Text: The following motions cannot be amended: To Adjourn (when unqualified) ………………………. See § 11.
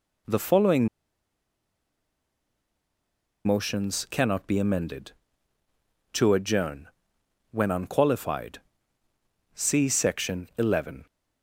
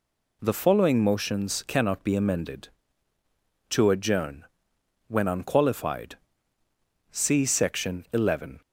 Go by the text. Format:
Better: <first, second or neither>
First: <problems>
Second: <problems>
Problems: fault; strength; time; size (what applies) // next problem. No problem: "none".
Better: second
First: pauses between "following" and "motions"; strong; at 0.8 s; 2.5 s long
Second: none